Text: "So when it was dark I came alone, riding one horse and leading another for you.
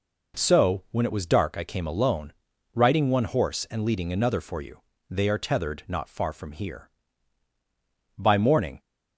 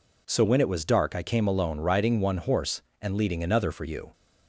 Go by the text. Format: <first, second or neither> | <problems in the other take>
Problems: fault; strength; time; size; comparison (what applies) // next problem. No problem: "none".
second | goes on to say "They are tethered not far from here By morning"; strong; from 5.0 s on; 3.7 s long